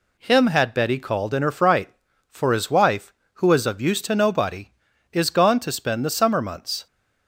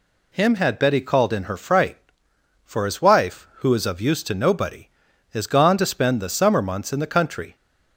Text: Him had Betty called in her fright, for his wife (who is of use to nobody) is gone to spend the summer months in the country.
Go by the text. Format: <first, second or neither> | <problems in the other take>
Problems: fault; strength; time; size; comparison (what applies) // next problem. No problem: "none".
second | stops before "in the country"; at 6.8 s